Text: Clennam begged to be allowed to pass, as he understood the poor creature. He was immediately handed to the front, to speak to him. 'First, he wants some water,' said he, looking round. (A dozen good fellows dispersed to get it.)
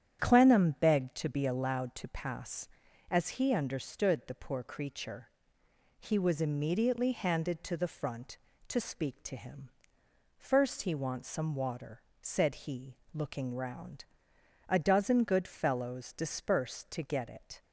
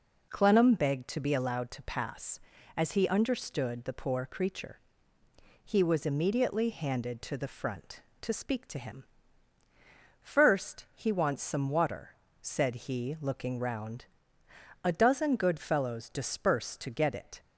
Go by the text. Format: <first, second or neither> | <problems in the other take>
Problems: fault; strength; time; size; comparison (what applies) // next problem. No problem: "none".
second | starts louder than the rest; strong; until 1.2 s; 9.5 dB